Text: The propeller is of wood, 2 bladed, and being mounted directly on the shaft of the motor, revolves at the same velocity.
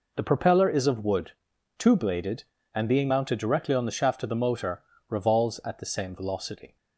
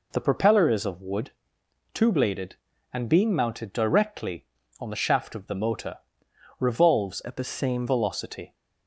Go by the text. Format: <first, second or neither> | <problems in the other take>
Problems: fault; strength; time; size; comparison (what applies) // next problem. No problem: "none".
first | changes voice from "at" to "same"; from 7.2 to 7.8 s; 0.6 s long